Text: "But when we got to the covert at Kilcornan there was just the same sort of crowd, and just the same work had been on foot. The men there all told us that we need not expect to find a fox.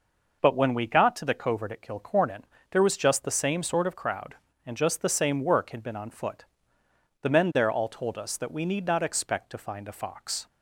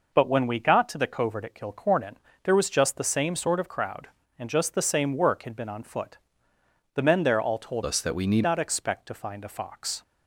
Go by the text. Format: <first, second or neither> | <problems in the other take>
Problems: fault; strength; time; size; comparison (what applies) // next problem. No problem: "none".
first | pauses between "Kilcornan" and "there"; slight; at 2.1 s; 0.28 s long; slight in the first // changes voice from "us" to "need"; from 7.8 to 8.4 s; 0.6 s long